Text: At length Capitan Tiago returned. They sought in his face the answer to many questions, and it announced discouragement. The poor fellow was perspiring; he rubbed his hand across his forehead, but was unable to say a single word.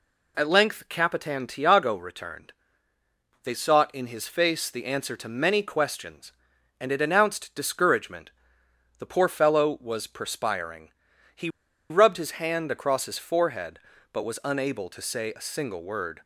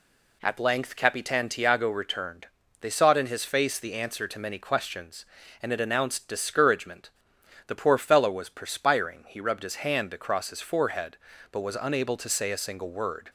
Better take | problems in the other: second | pauses between "he" and "rubbed"; at 11.4 s; 0.42 s long

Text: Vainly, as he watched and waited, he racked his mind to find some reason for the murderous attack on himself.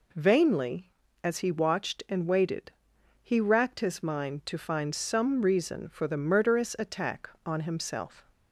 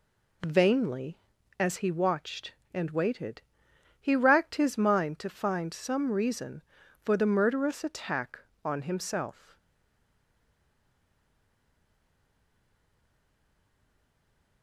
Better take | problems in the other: first | stays silent after the last word; strong; from 9.5 s on; 5.1 s long

